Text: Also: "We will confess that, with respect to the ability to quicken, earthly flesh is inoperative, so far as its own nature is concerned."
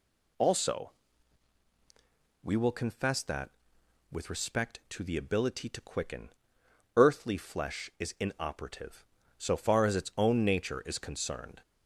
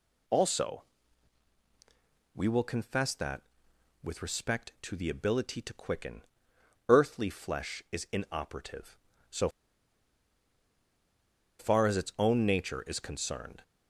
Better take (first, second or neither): first